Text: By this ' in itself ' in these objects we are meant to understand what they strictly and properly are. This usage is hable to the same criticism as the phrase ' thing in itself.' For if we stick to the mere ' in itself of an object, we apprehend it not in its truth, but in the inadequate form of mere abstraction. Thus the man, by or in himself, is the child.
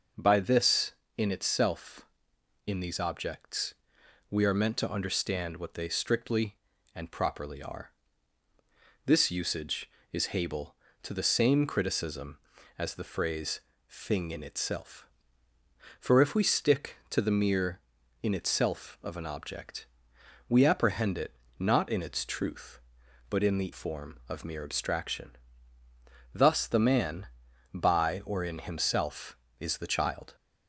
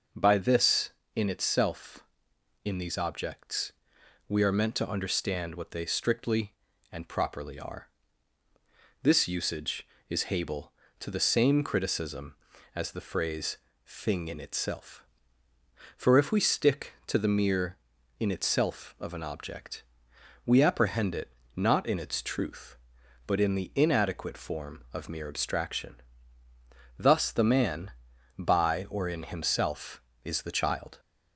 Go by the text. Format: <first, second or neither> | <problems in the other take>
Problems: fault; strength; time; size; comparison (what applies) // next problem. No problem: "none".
second | starts louder than the rest; noticeable; until 1.2 s; 6 dB; noticeable in the second // pauses between "objects" and "we"; noticeable; at 3.7 s; 0.56 s long; noticeable in the second // pauses between "it" and "not"; slight; at 21.3 s; 0.24 s long; slight in the second // skips "inadequate"; at 23.7 s